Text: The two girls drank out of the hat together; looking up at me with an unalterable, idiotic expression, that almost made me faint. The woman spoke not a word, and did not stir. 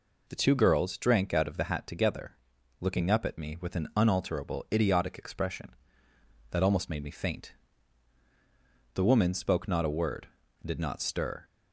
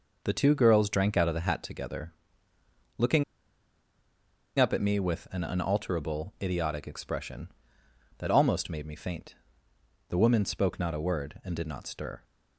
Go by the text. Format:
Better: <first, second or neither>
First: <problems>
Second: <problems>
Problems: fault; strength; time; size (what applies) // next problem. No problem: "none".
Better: first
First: none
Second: pauses between "looking" and "up"; strong; at 3.2 s; 1.3 s long